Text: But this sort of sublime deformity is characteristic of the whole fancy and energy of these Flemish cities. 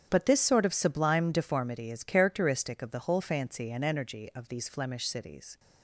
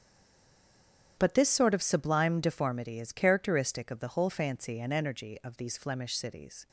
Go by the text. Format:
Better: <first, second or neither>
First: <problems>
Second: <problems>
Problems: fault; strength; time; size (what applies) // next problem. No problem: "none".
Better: first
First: starts louder than the rest; strong; until 1.1 s; 8.5 dB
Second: stays silent before the first word; noticeable; until 1.1 s; 1.1 s long // starts louder than the rest; strong; until 2.1 s; 8.5 dB